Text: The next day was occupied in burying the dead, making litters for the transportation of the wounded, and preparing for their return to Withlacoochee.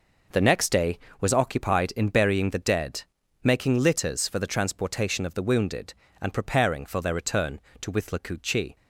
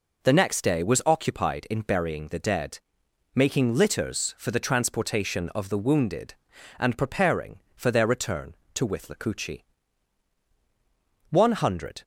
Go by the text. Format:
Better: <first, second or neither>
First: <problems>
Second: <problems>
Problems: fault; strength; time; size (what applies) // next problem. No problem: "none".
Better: first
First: none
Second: goes on to say "One hundred"; noticeable; from 11.3 s on; 0.72 s long